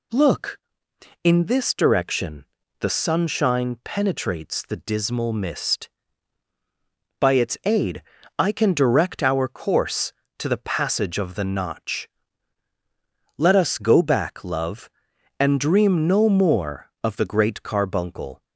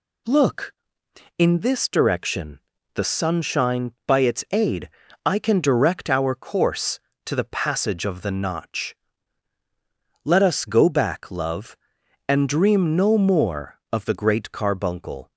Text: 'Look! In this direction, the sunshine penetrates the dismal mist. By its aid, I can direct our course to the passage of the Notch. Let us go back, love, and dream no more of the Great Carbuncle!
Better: first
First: none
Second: skips "penetrates the dismal mist"; at 3.9 s

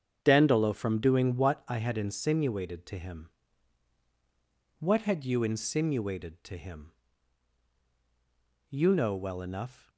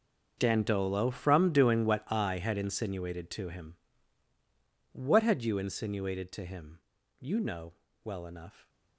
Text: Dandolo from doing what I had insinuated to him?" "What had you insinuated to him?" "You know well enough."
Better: first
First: starts louder than the rest; strong; until 1.2 s; 7.5 dB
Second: gets quieter; strong; throughout; 16.5 dB // starts louder than the rest; until 1.3 s; 6 dB // pauses between "know" and "well"; slight; at 7.7 s; 0.32 s long

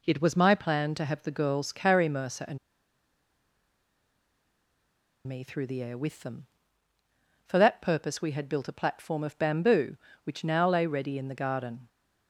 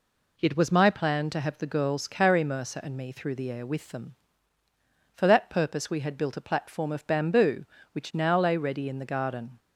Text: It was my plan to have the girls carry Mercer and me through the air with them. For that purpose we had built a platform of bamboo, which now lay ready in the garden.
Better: second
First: pauses between "and" and "me"; strong; at 2.5 s; 2.6 s long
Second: none

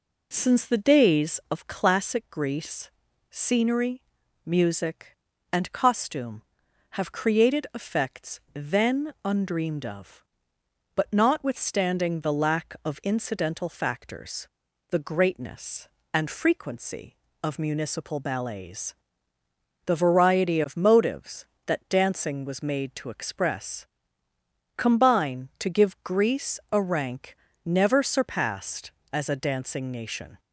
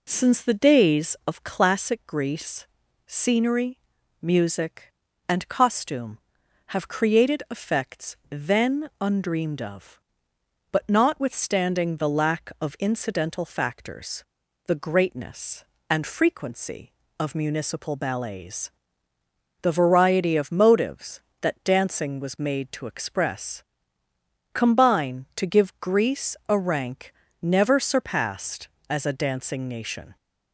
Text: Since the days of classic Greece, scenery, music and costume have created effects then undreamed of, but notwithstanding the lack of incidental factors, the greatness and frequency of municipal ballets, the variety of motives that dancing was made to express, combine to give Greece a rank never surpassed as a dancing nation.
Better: neither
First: pauses between "rank" and "never"; slight; at 27.3 s; 0.26 s long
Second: pauses between "rank" and "never"; slight; at 27.1 s; 0.26 s long

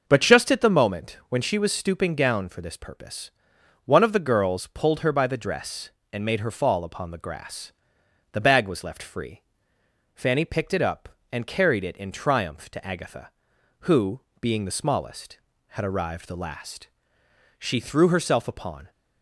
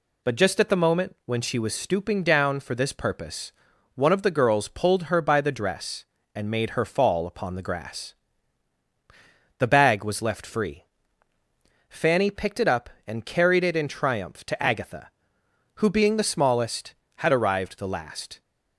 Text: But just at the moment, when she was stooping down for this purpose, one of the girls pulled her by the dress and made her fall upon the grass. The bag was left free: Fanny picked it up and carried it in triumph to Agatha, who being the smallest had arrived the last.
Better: second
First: starts louder than the rest; noticeable; until 1.0 s; 6 dB // pauses between "who" and "being"; slight; at 14.2 s; 0.20 s long // goes on to say "She threw herself upon"; from 17.5 s on; 1.3 s long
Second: none

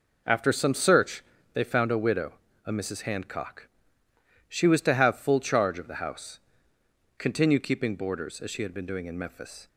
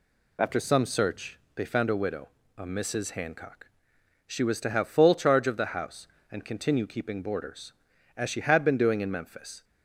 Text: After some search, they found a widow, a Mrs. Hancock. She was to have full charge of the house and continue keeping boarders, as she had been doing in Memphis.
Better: second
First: skips "and"; at 6.7 s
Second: none

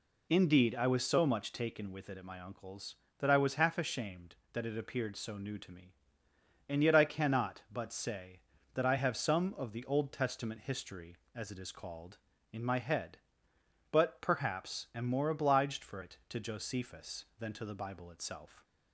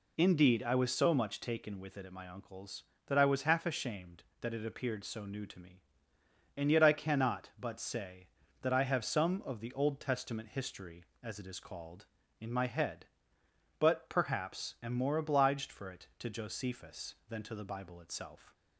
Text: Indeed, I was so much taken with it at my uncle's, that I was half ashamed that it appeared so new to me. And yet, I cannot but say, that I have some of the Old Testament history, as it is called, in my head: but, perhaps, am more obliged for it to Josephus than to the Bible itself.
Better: neither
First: none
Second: none

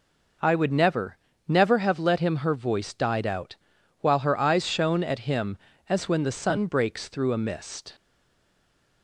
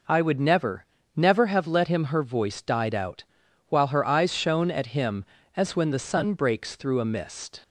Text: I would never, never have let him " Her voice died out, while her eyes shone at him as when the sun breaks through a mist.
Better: second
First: stays silent after the last word; from 7.9 s on; 1.1 s long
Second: none

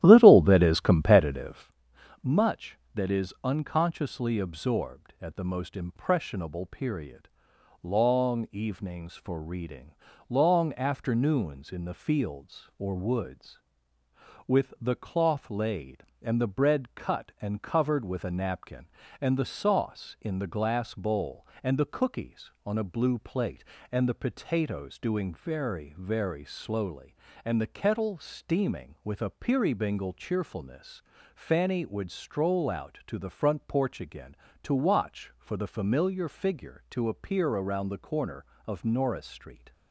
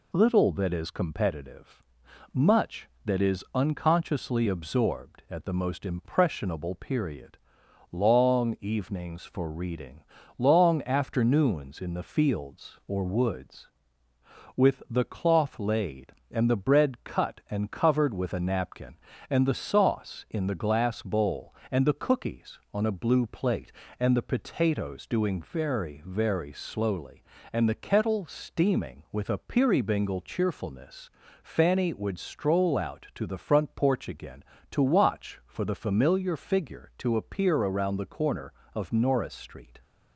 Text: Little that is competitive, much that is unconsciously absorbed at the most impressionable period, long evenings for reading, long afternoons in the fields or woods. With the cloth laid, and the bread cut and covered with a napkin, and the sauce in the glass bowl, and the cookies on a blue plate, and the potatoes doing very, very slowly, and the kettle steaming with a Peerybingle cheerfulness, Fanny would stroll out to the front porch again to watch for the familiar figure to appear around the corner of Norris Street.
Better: second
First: starts louder than the rest; strong; until 1.7 s; 12 dB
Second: none

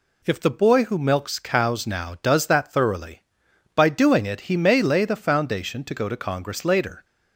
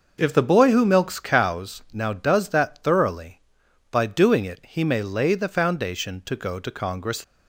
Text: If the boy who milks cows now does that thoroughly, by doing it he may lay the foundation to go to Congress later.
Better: first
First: none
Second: stops before "later"; at 7.2 s

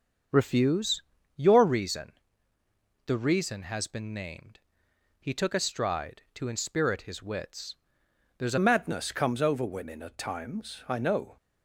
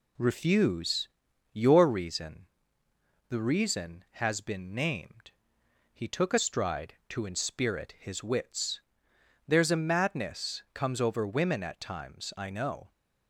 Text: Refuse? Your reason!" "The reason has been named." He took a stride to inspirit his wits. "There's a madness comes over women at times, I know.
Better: second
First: starts louder than the rest; until 1.6 s; 7 dB // changes voice at "madness"; from 8.5 s on; 2.8 s long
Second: none

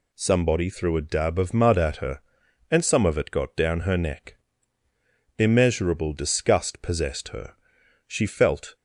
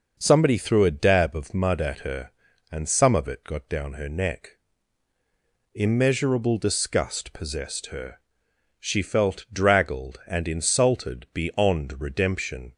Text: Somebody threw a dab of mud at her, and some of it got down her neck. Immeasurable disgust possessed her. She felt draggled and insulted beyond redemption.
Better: second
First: stops before "draggled and insulted beyond redemption"; at 8.7 s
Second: none

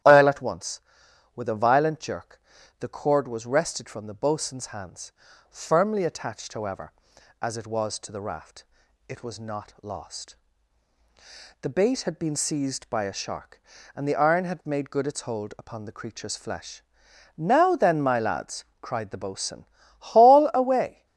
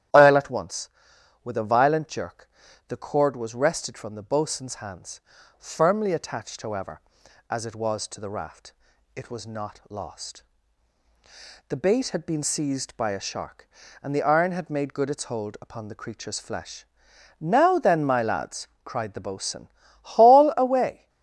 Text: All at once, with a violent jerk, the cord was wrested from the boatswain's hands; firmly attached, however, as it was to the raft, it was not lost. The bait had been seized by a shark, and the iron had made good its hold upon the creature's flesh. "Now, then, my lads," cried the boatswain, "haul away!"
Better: neither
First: starts louder than the rest; strong; until 1.5 s; 11.5 dB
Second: starts louder than the rest; strong; until 1.6 s; 11.5 dB

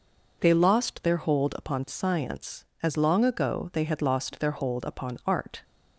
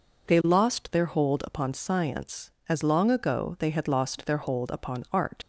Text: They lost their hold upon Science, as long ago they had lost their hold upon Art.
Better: first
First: none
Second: leaves "Art" unfinished; at 5.4 s; 75 ms

